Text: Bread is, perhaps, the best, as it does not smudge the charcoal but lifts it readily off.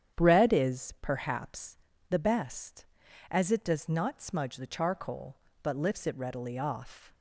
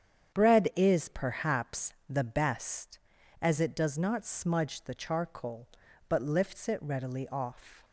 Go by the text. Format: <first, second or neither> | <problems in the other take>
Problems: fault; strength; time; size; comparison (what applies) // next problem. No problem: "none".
neither | starts louder than the rest; strong; the same in both